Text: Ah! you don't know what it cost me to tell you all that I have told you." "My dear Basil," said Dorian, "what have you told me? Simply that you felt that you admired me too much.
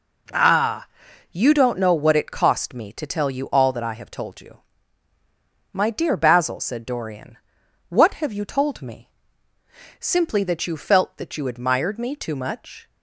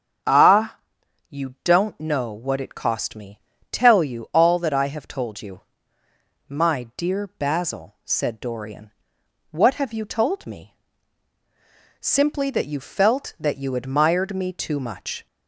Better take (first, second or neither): first